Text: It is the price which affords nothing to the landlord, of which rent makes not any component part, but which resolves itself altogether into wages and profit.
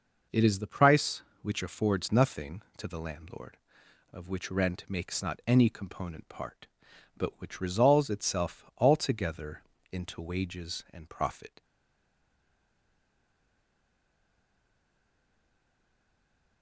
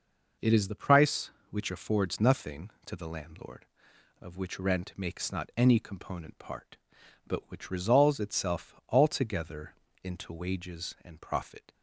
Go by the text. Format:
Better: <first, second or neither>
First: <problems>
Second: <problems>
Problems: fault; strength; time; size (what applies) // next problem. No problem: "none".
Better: second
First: pauses between "altogether" and "into"; slight; at 9.6 s; 0.30 s long // stays silent after the last word; strong; from 11.6 s on; 5.0 s long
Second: pauses between "altogether" and "into"; slight; at 9.7 s; 0.30 s long